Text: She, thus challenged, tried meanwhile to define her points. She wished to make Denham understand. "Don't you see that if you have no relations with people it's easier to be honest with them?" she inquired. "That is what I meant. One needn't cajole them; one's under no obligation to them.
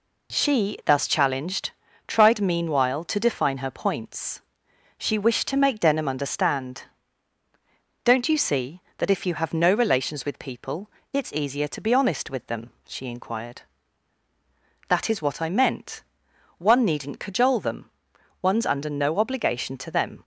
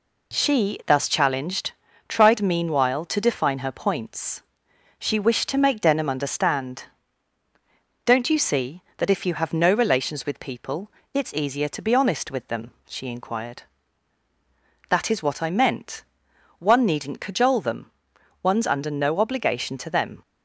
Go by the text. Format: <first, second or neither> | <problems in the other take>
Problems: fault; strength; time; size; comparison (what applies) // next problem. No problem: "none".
neither | pauses between "people" and "it's"; slight; the same in both